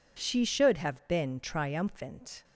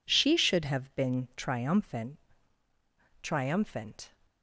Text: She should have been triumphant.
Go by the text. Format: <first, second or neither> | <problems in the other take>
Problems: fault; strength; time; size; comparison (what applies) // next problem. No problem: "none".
first | says "triumphant" twice; at 3.2 s